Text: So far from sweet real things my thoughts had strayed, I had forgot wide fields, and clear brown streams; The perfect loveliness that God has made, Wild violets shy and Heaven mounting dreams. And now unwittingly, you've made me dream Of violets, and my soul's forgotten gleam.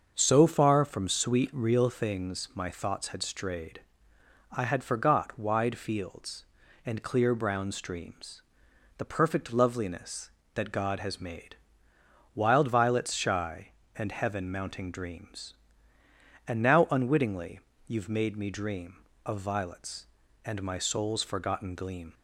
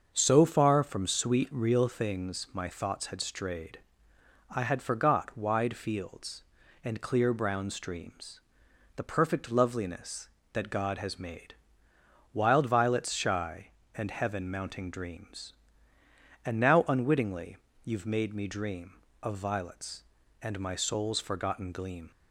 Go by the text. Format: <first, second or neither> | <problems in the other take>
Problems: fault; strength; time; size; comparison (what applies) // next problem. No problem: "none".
neither | starts louder than the rest; the same in both